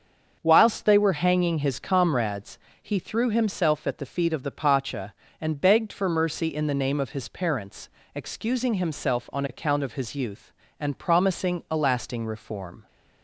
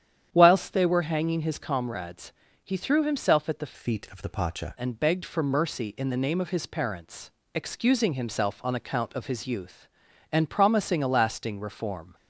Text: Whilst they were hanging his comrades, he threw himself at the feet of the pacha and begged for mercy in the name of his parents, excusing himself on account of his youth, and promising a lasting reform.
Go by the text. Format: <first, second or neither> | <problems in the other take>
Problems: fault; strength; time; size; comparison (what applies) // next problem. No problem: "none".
first | starts louder than the rest; strong; until 1.3 s; 9.5 dB; also in the first // changes voice from "feet" to "pacha"; from 3.7 to 4.7 s; 1.0 s long